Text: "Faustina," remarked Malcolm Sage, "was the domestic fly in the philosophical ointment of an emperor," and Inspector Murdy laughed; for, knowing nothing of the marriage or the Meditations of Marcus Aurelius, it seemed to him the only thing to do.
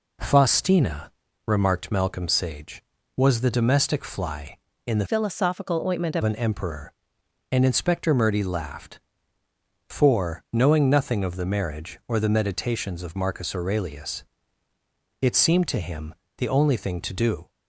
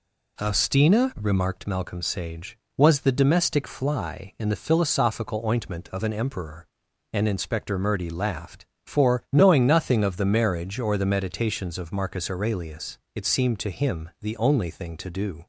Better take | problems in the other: second | changes voice from "philosophical" to "of"; from 5.0 to 6.2 s; 1.2 s long // pauses between "him" and "the"; slight; at 16.1 s; 0.24 s long

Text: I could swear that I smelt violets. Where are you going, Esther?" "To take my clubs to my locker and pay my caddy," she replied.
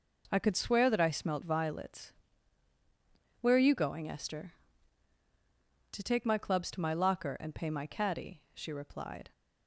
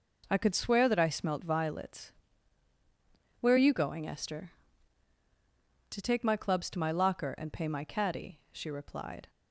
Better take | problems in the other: neither | none

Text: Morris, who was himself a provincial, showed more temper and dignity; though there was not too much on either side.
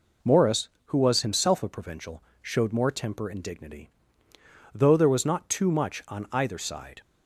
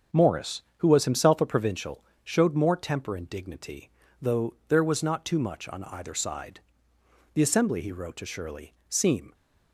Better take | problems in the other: first | starts louder than the rest; strong; until 1.3 s; 7.5 dB // pauses between "though" and "there"; slight; at 4.5 s; 0.16 s long // goes on to say "The Assembly he wrote to Shirley seem"; strong; from 7.3 s on; 2.0 s long

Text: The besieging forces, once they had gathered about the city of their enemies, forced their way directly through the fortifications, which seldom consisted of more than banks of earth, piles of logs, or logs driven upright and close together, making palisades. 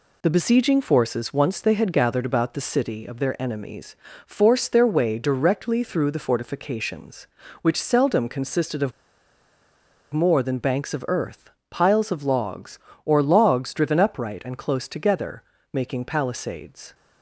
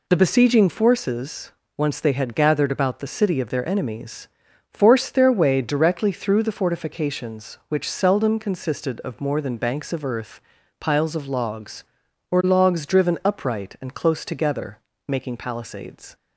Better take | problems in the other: second | pauses between "of" and "more"; at 8.9 s; 1.2 s long

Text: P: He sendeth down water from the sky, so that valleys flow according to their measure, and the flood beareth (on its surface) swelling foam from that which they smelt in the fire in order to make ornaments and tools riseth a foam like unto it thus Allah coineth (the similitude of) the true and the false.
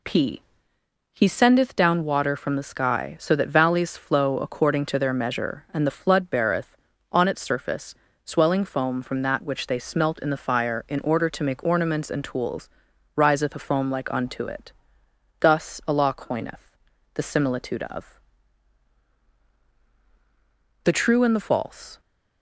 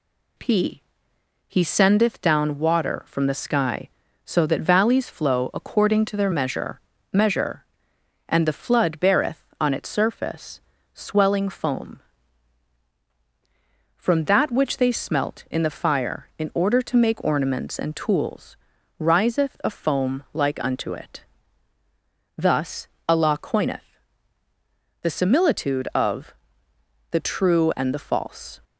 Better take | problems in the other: first | says "measure" twice; at 7.1 s // pauses between "tools" and "riseth"; at 18.5 s; 0.44 s long; noticeable in the first // pauses between "it" and "thus"; at 21.2 s; 1.1 s long; noticeable in the first // pauses between "thus" and "Allah"; slight; at 22.8 s; 0.20 s long

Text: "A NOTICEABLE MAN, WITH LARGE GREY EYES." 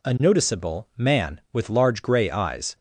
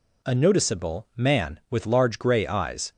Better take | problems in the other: neither | none

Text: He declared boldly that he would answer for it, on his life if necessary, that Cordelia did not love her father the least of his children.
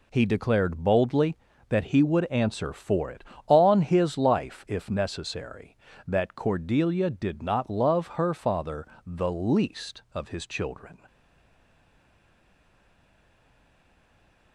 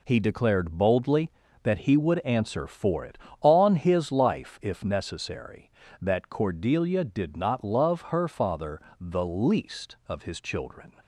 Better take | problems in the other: second | pauses between "father" and "the"; slight; at 8.8 s; 0.22 s long; slight in the second // stays silent after the last word; strong; from 11.0 s on; 3.5 s long

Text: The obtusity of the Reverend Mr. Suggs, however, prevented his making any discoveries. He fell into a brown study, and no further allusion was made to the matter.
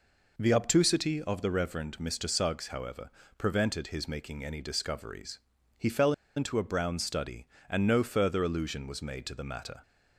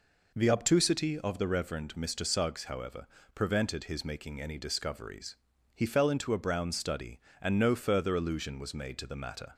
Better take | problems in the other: second | pauses between "fell" and "into"; slight; at 6.1 s; 0.24 s long

